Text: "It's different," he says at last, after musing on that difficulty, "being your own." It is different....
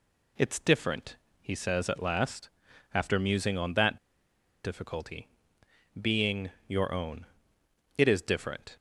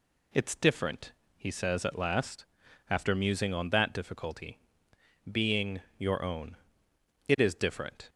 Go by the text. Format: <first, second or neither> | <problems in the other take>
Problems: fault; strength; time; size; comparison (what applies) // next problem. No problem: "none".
second | pauses between "that" and "difficulty"; noticeable; at 3.9 s; 0.67 s long // pauses between "being" and "your"; slight; at 6.5 s; 0.16 s long; slight in the second